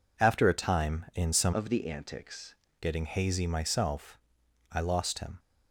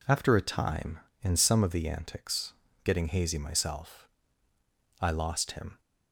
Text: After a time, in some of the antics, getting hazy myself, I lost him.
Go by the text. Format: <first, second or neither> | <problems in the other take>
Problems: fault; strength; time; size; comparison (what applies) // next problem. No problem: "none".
second | changes voice from "of" to "antics"; from 1.5 to 2.5 s; 1.0 s long